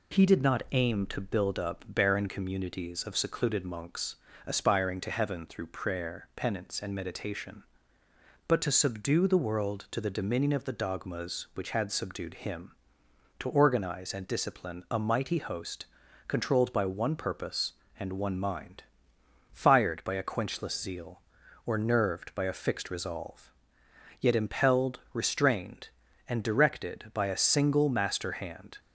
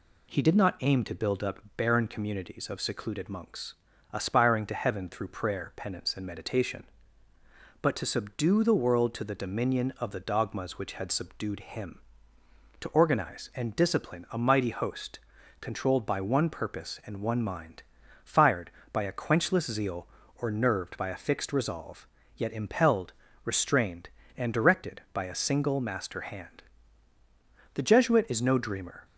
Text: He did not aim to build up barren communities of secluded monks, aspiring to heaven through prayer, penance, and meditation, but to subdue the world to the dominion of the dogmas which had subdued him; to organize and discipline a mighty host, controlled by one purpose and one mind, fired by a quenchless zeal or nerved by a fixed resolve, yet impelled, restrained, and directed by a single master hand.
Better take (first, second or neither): first